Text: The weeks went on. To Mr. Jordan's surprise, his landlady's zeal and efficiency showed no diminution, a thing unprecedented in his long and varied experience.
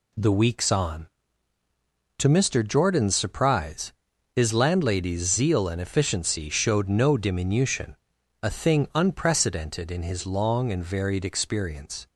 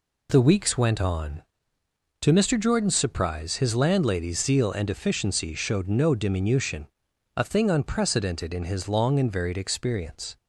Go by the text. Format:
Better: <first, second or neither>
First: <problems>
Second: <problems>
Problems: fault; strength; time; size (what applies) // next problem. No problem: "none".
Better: second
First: skips "went"; at 0.7 s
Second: none